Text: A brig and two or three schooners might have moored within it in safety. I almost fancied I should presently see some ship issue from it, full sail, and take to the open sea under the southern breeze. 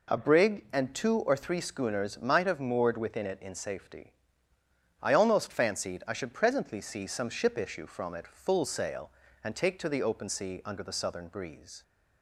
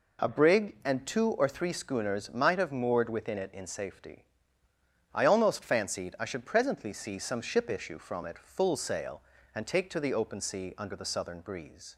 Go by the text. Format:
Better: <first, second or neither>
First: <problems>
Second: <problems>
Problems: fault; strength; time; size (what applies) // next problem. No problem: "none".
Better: neither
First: none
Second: none